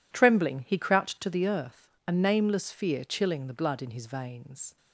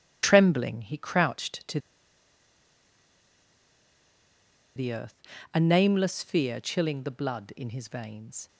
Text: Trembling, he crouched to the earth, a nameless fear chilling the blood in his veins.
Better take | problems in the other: first | pauses between "to" and "the"; strong; at 1.7 s; 2.9 s long

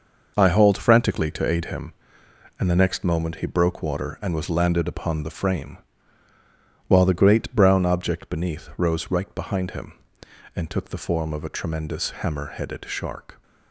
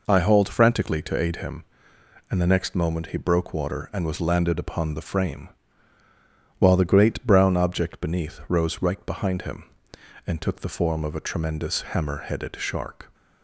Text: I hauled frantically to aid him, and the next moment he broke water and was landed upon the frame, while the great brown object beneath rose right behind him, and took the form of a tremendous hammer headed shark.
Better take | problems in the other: second | gets quieter; strong; throughout; 8 dB

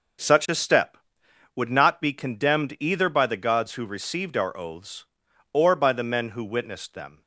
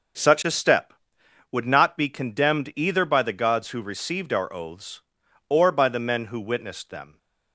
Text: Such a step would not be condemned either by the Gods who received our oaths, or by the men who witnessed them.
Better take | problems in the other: neither | starts louder than the rest; the same in both

